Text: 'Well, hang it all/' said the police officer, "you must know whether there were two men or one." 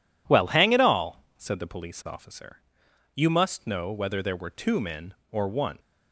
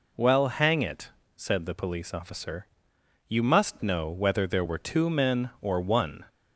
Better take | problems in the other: first | skips "all"; at 1.2 s

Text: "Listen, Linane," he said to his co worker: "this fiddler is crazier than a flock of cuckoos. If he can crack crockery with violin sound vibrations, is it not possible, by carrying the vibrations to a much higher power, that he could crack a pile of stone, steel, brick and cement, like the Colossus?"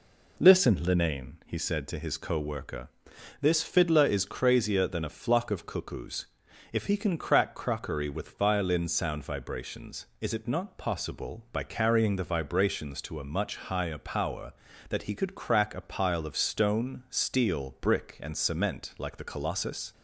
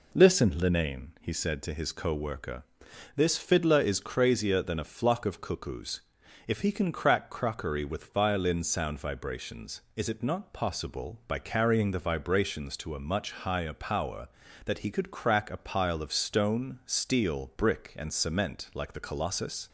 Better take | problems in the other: neither | none

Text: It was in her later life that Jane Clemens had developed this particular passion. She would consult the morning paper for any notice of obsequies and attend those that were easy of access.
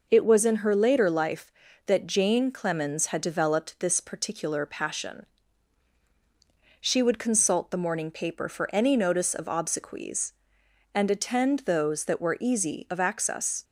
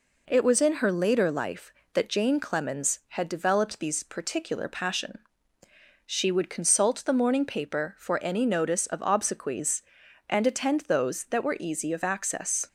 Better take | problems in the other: first | says "these" for "this"; at 3.7 s

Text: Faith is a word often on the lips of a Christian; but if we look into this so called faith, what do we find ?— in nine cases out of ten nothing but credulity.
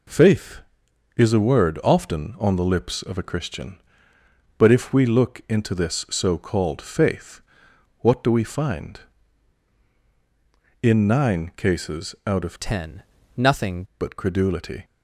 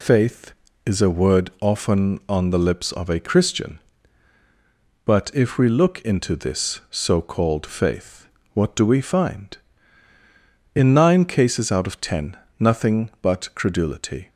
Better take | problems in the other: second | changes voice from "ten" to "nothing"; from 12.5 to 13.8 s; 1.3 s long // pauses between "ten" and "nothing"; slight; at 13.0 s; 0.32 s long; slight in the second

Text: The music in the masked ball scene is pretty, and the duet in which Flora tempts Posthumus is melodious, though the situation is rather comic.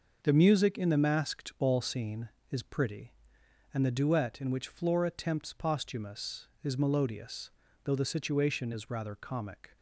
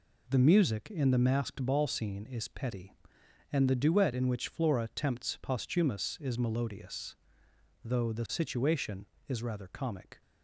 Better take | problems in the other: first | says "petty" for "pretty"; at 2.4 s

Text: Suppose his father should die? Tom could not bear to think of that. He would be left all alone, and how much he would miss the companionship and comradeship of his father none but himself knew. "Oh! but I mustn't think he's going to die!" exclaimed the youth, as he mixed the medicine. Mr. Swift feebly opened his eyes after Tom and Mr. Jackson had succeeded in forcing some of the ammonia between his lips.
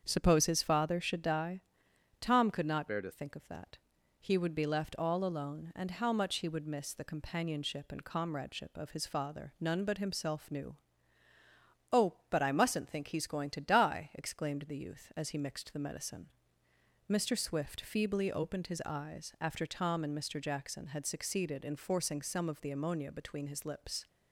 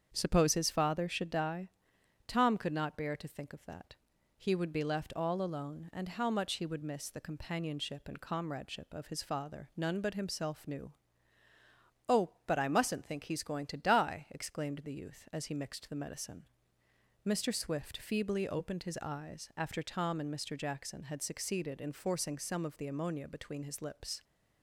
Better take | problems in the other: second | starts louder than the rest; strong; until 1.0 s; 7.5 dB; strong in the second // changes voice from "bear" to "to"; from 2.8 to 3.1 s; 0.3 s long

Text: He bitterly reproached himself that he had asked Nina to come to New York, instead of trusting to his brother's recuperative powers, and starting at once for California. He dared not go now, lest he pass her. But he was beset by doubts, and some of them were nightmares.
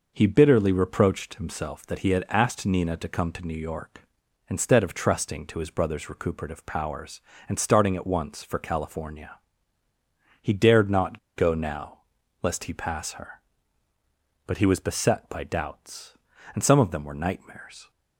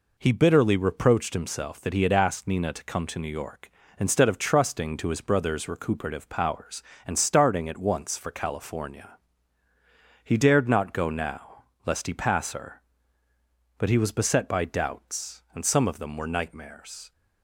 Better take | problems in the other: second | pauses between "not" and "go"; slight; at 11.1 s; 0.16 s long

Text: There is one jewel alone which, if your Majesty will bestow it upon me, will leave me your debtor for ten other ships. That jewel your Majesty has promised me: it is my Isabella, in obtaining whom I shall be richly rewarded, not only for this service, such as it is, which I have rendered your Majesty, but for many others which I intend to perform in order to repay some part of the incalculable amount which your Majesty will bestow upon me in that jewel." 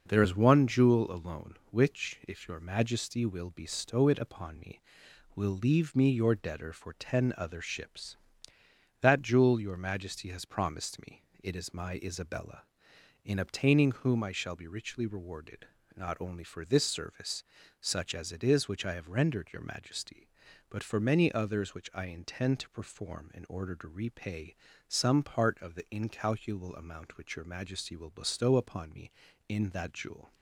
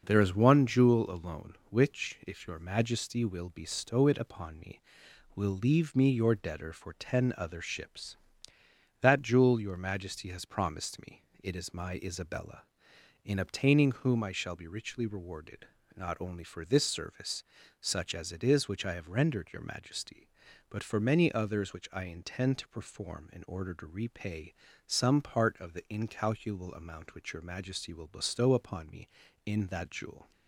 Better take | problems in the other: neither | pauses between "repay" and "some"; slight; the same in both

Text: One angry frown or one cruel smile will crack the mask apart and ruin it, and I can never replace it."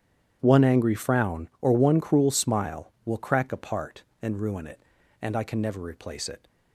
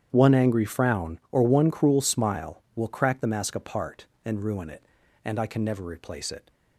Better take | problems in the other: second | starts louder than the rest; strong; until 1.4 s; 9.5 dB; strong in the second // skips "the mask"; at 3.5 s

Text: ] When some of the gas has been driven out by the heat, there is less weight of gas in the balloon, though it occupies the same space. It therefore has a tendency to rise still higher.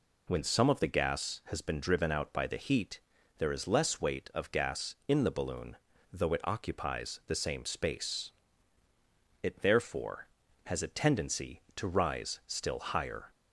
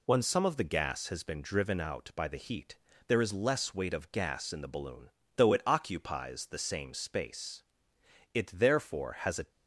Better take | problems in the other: first | stops before "tendency to rise still higher"; at 9.4 s

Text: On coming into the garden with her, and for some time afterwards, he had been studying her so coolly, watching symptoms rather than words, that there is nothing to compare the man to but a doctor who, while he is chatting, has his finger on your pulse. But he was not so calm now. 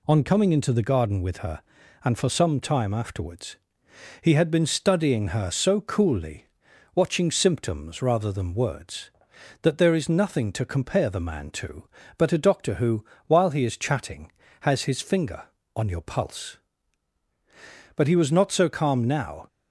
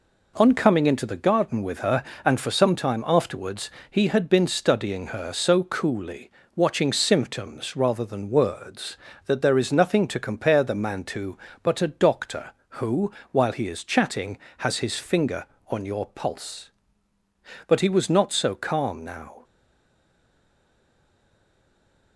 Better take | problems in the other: first | stays silent after the last word; strong; from 19.4 s on; 2.7 s long

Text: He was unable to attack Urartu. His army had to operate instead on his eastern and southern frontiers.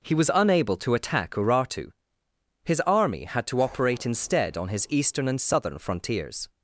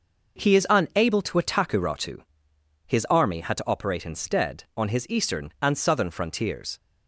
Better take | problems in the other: first | says "is" for "was"; at 0.5 s

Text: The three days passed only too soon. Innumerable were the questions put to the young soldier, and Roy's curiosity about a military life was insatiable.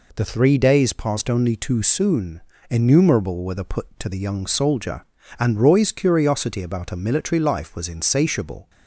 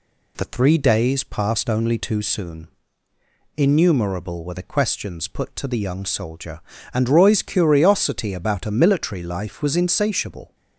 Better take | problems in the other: second | skips "questions"; at 3.6 s

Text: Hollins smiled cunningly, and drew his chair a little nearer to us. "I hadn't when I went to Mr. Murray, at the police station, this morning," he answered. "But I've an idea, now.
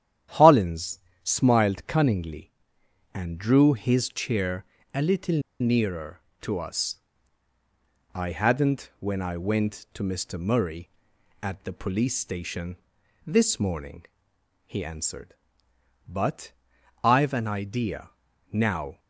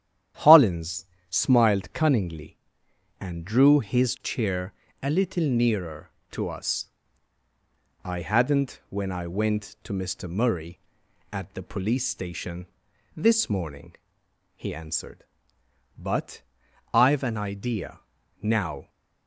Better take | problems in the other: second | starts louder than the rest; strong; until 1.5 s; 10.5 dB; strong in the second // pauses between "Hollins" and "smiled"; slight; at 0.9 s; 0.26 s long; slight in the second // pauses between "chair" and "a"; slight; at 4.6 s; 0.26 s long; slight in the second // pauses between "little" and "nearer"; slight; at 5.4 s; 0.19 s long // pauses between "But" and "I've"; noticeable; at 16.5 s; 0.50 s long; noticeable in the second

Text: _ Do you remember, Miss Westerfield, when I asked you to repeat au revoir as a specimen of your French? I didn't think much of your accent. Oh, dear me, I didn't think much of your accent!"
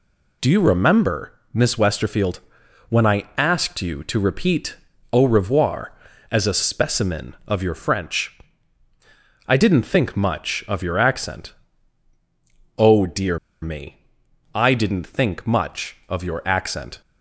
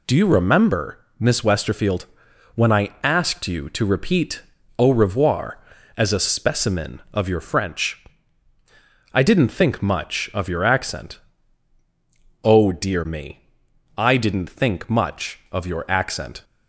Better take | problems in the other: second | pauses between "repeat" and "au"; slight; at 4.7 s; 0.34 s long; slight in the second // pauses between "dear" and "me"; slight; at 13.3 s; 0.24 s long

